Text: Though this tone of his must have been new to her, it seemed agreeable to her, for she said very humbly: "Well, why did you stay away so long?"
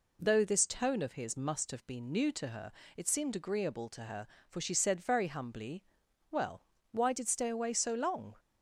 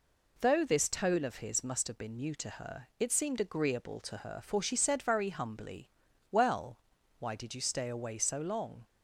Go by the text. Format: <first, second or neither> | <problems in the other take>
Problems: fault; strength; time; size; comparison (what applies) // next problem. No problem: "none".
second | skips "you"; at 7.2 s